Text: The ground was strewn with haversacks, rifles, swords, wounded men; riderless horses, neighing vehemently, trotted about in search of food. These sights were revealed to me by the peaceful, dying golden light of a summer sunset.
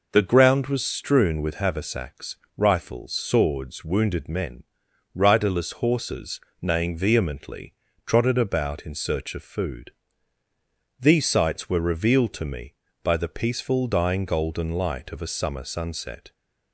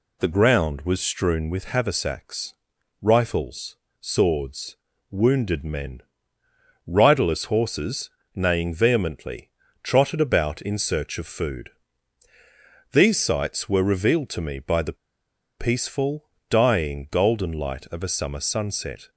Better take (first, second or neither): first